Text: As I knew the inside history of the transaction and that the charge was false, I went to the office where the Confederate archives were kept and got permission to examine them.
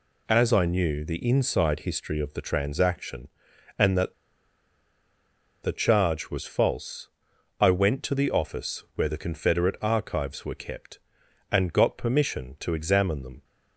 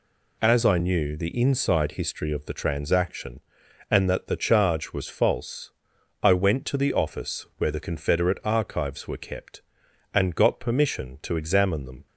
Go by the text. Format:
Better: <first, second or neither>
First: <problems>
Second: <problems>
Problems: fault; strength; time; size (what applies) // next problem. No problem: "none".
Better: second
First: pauses between "that" and "the"; strong; at 4.1 s; 1.4 s long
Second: none